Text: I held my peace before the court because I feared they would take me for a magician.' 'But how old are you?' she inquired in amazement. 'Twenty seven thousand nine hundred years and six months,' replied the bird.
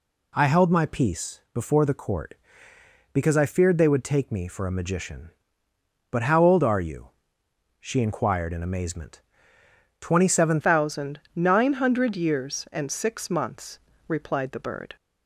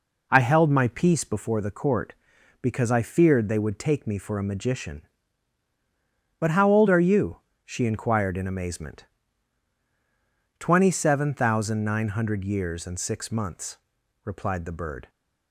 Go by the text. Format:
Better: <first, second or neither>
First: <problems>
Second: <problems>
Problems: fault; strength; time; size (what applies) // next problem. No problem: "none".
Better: second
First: changes voice at "thousand"; from 10.6 s on; 4.3 s long // pauses between "thousand" and "nine"; slight; at 11.1 s; 0.16 s long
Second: none